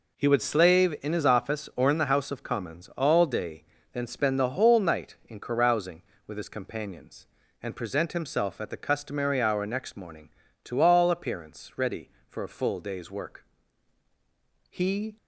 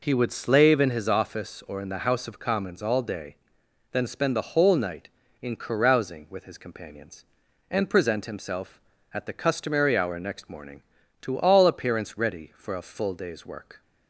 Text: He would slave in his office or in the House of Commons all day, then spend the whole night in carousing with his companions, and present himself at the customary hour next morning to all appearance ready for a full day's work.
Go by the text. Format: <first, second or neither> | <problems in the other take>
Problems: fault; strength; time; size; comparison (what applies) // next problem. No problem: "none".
second | goes on to say "He"; slight; from 14.7 s on; 0.46 s long